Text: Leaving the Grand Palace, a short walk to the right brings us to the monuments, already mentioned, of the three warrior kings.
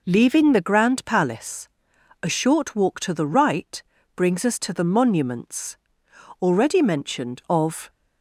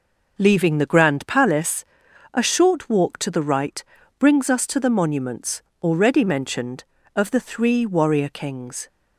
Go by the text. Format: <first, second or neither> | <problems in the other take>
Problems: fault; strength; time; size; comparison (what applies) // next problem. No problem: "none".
second | pauses between "right" and "brings"; slight; at 3.8 s; 0.36 s long; slight in the second // stops before "the three warrior kings"; at 7.8 s